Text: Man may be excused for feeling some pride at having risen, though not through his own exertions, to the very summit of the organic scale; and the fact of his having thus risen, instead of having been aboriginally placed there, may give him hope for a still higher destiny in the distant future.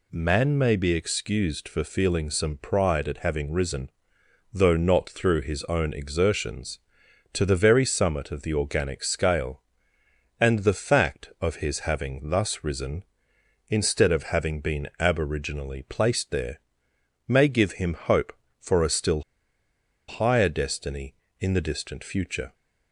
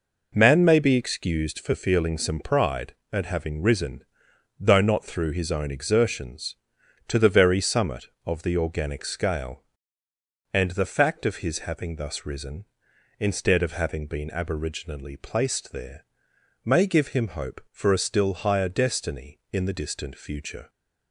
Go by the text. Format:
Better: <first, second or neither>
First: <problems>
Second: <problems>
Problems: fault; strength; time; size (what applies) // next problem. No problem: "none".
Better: second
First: pauses between "still" and "higher"; noticeable; at 19.2 s; 0.87 s long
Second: none